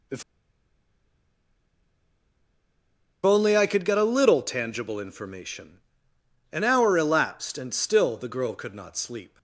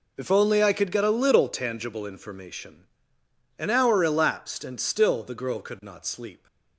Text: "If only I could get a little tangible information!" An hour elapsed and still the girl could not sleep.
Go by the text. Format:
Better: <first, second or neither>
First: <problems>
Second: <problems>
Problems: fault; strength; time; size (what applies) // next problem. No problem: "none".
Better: second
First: pauses between "If" and "only"; strong; at 0.2 s; 3.0 s long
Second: none